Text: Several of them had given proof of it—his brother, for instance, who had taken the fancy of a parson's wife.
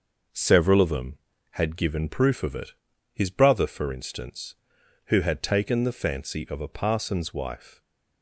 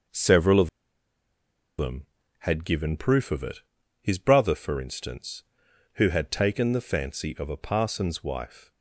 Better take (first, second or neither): first